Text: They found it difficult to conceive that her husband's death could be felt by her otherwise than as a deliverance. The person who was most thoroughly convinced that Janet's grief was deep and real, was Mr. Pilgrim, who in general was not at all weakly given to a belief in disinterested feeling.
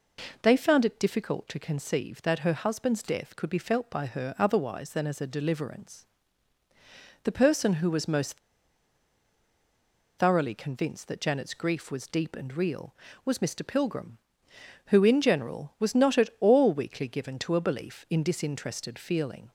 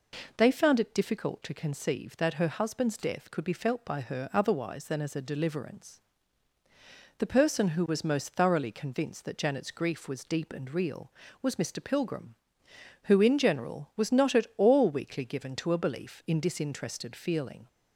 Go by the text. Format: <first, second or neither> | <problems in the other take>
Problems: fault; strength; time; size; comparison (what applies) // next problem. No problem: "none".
second | pauses between "most" and "thoroughly"; strong; at 8.3 s; 1.8 s long